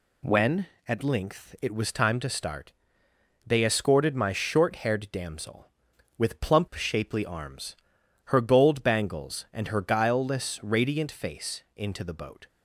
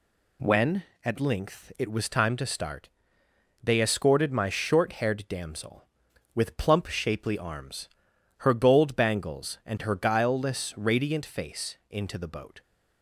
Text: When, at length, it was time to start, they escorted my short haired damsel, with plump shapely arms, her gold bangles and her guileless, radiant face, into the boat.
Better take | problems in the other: neither | none

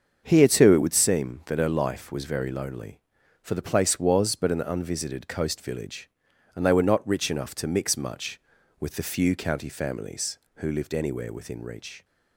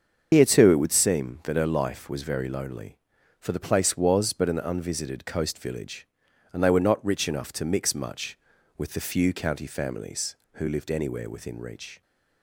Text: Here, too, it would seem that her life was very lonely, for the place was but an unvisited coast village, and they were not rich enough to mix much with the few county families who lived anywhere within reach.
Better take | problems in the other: first | loses the start of "Here"; at 0.3 s; 90 ms // starts louder than the rest; until 1.3 s; 7 dB; also in the first

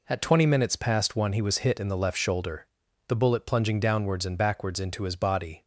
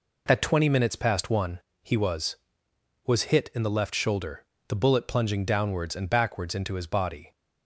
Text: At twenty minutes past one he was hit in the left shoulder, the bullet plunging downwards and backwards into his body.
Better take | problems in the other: first | pauses between "one" and "he"; slight; at 1.6 s; 0.22 s long // says "was" twice; at 3.0 s

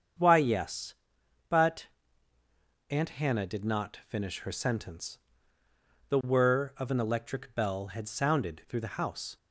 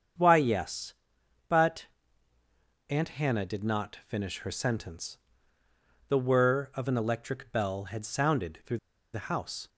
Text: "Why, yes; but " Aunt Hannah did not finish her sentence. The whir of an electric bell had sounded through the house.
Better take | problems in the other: first | starts louder than the rest; strong; until 1.7 s; 7.5 dB; strong in the first // pauses between "through" and "the"; slight; at 8.7 s; 0.35 s long

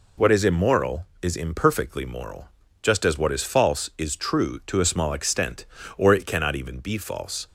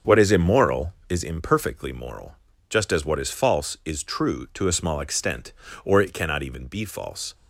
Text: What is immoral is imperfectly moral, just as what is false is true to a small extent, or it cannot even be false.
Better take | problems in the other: first | starts louder than the rest; until 1.3 s; 7 dB

